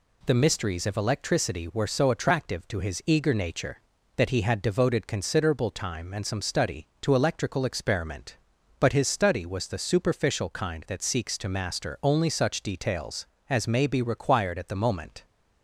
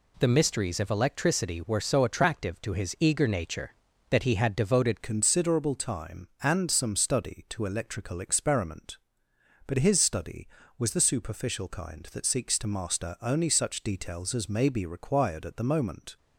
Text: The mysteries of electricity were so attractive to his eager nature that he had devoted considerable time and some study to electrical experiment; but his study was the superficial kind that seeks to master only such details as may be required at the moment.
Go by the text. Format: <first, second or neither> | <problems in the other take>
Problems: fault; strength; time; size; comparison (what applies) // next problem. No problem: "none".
first | changes voice at "considerable"; from 5.0 s on; 11.1 s long